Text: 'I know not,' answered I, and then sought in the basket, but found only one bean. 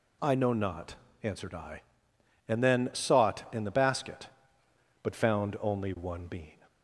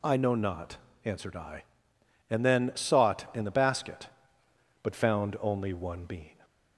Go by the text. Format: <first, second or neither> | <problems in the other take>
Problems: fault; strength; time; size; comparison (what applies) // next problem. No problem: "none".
neither | none